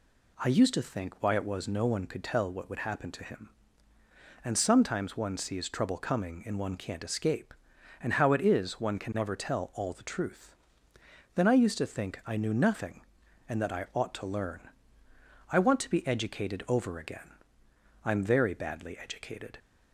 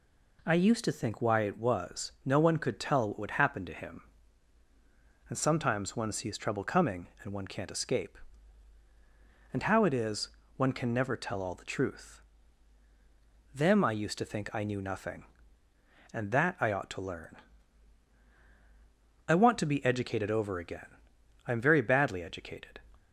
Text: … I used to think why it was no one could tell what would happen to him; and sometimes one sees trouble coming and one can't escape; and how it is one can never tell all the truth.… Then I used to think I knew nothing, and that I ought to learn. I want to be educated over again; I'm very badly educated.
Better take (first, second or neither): first